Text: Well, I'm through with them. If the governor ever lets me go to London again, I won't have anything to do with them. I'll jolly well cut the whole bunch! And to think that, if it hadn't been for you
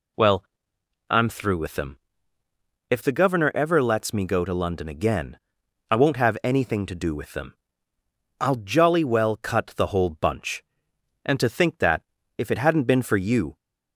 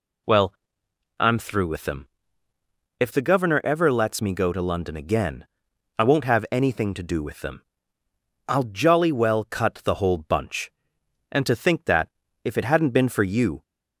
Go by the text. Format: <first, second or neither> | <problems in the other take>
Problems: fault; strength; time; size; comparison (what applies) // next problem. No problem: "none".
neither | none